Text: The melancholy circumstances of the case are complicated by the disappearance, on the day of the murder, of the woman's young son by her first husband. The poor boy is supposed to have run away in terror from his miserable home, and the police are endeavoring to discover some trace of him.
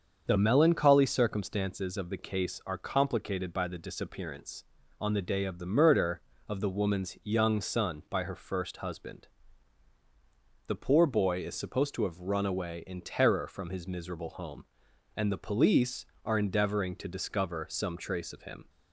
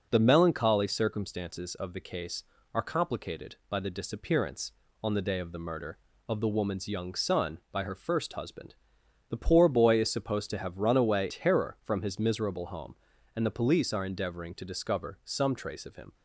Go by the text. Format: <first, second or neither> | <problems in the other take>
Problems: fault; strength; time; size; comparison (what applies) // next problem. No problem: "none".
first | starts louder than the rest; until 1.1 s; 6 dB; also in the first // skips "in"; at 11.3 s